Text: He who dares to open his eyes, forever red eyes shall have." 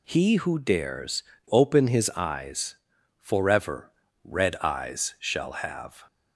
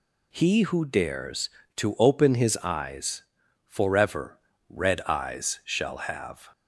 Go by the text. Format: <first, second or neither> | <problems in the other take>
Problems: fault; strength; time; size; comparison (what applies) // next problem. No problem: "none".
second | skips "to"; at 1.3 s // pauses between "forever" and "red"; slight; at 3.9 s; 0.34 s long; slight in the second